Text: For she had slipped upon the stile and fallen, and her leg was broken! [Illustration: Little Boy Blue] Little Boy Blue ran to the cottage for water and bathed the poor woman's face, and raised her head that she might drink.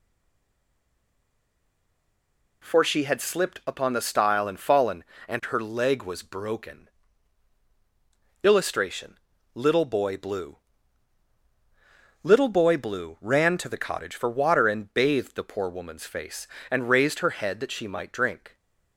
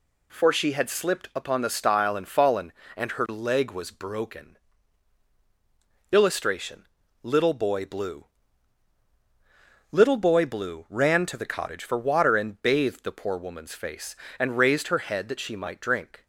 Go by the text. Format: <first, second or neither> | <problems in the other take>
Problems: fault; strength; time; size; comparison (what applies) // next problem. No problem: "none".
second | stays silent before the first word; strong; until 2.6 s; 2.6 s long // pauses between "Blue" and "Little"; strong; at 10.5 s; 1.6 s long; strong in the second